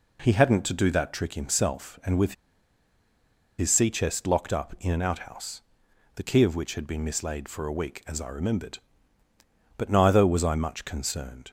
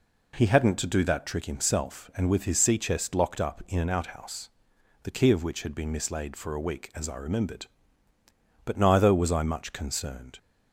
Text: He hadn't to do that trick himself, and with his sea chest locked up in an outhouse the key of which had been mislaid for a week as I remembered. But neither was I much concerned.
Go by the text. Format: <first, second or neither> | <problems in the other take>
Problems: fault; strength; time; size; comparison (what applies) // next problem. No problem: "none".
second | pauses between "with" and "his"; strong; at 2.3 s; 1.2 s long // pauses between "outhouse" and "the"; noticeable; at 5.5 s; 0.56 s long; noticeable in the second